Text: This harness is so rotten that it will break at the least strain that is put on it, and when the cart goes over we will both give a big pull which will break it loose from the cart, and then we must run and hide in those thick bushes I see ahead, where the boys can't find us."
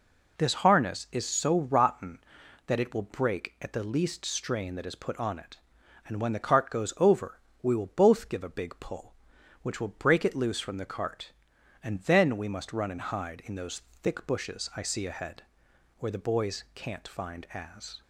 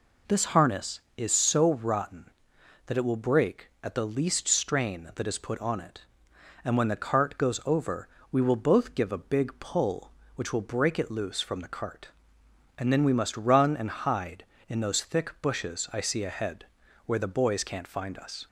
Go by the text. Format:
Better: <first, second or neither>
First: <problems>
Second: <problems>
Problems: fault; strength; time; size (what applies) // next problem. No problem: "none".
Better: second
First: pauses between "over" and "we"; slight; at 7.3 s; 0.22 s long // pauses between "those" and "thick"; slight; at 13.8 s; 0.20 s long // says "as" for "us"; at 17.5 s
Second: pauses between "over" and "we"; slight; at 8.0 s; 0.22 s long